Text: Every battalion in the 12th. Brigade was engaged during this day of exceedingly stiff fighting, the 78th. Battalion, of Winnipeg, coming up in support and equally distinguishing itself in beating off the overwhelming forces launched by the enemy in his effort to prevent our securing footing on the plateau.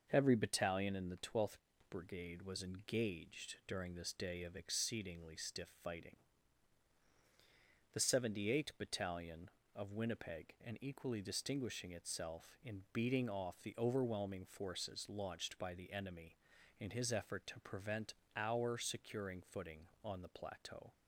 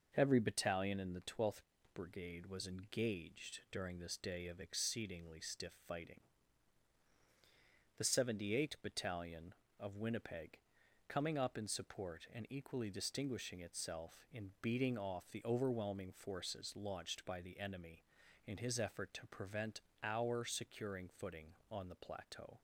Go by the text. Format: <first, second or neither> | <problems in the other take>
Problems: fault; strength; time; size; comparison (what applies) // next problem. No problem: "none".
second | skips "coming up in support"; at 10.5 s // pauses between "prevent" and "our"; slight; at 18.1 s; 0.20 s long; slight in the second